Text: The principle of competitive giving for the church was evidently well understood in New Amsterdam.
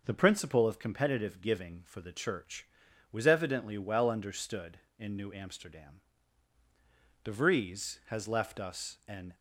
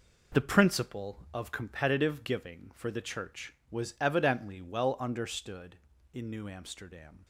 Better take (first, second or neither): second